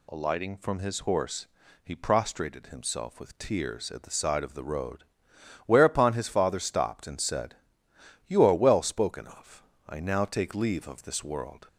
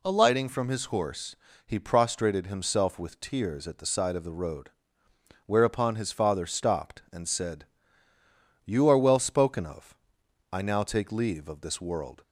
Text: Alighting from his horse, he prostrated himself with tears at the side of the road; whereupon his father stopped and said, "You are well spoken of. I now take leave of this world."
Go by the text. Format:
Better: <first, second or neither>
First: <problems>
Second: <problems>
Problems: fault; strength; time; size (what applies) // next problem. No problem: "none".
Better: neither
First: none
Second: none